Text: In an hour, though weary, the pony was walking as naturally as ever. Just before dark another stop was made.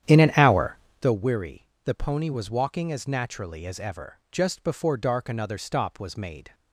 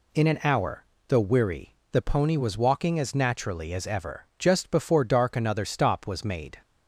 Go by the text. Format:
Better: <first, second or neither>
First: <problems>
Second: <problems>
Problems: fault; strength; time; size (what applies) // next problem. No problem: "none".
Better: second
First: starts louder than the rest; strong; until 1.2 s; 10 dB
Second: none